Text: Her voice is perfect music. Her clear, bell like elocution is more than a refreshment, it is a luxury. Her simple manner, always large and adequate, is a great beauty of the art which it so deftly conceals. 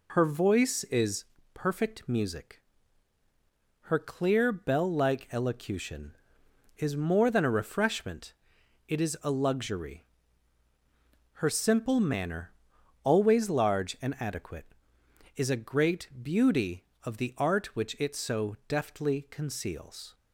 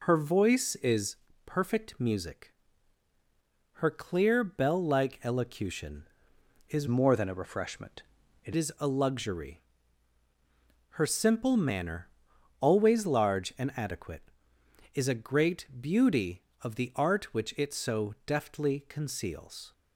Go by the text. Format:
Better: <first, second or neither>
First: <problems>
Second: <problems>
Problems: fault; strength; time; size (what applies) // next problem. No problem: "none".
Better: first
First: pauses between "is" and "perfect"; slight; at 1.2 s; 0.30 s long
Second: pauses between "is" and "perfect"; slight; at 1.1 s; 0.30 s long // changes voice from "more" to "it"; from 6.8 to 8.5 s; 1.7 s long